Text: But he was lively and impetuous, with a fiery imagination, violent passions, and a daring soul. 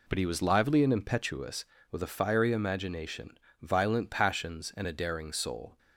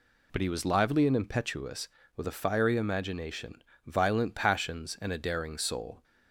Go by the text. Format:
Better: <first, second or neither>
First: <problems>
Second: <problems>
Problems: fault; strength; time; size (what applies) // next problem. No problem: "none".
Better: second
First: gets quieter; strong; throughout; 8 dB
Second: none